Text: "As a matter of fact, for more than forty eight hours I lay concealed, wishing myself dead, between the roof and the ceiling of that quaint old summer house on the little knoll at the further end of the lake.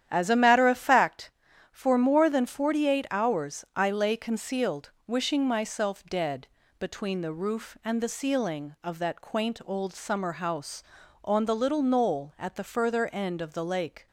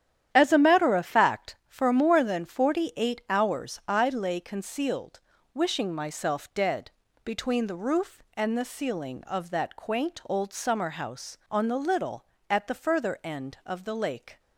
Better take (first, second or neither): first